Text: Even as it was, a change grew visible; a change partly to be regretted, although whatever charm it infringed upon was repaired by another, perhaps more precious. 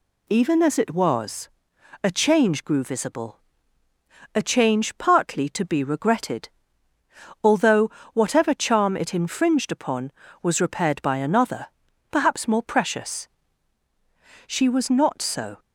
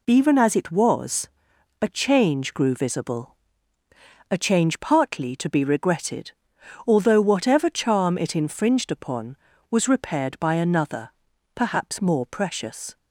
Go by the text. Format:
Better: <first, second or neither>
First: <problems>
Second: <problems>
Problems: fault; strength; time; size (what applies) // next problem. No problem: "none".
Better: second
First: pauses between "although" and "whatever"; slight; at 7.9 s; 0.24 s long // goes on to say "She was not so"; noticeable; from 14.4 s on; 1.1 s long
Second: none